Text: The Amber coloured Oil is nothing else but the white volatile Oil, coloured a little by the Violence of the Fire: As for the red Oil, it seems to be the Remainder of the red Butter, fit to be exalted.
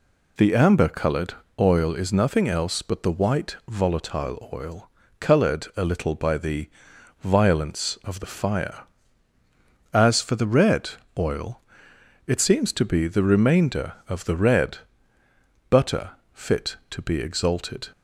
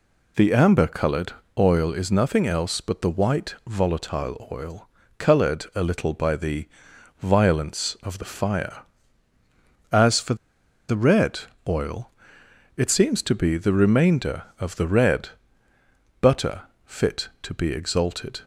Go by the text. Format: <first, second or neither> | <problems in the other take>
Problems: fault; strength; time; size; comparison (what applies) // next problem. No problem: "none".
first | pauses between "coloured" and "Oil"; slight; at 1.3 s; 0.24 s long; slight in the first // pauses between "the" and "Violence"; noticeable; at 6.6 s; 0.54 s long; noticeable in the first // pauses between "for" and "the"; noticeable; at 10.3 s; 0.54 s long // pauses between "red" and "Oil"; slight; at 11.3 s; 0.28 s long; slight in the first // pauses between "red" and "Butter"; noticeable; at 15.2 s; 0.92 s long; noticeable in the first